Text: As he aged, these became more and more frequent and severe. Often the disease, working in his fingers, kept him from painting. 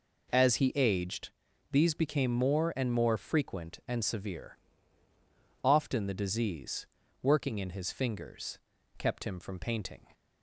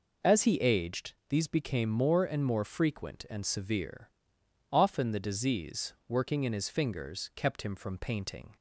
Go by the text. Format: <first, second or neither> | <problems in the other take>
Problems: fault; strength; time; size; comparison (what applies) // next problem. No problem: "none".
neither | none